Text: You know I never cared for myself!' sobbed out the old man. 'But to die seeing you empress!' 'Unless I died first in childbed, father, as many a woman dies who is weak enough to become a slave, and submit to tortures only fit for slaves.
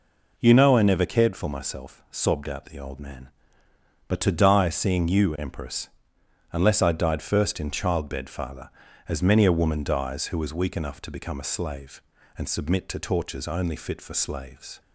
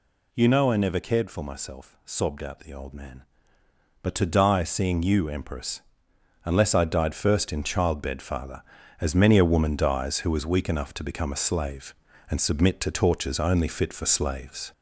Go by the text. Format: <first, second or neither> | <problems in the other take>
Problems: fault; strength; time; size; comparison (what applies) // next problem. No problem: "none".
first | gets louder; throughout; 3.5 dB